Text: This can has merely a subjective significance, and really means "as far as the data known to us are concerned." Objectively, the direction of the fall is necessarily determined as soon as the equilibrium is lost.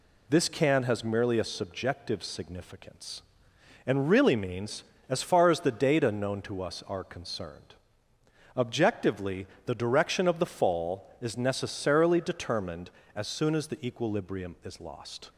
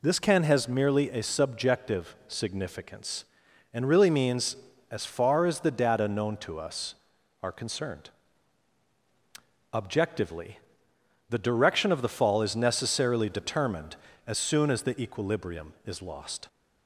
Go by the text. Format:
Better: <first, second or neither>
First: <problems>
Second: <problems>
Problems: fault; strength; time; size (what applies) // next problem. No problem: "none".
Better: neither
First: none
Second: none